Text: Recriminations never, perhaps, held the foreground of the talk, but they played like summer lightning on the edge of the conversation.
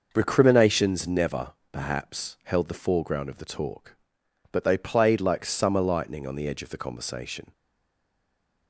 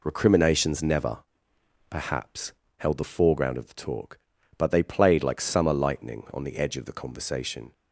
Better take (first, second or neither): second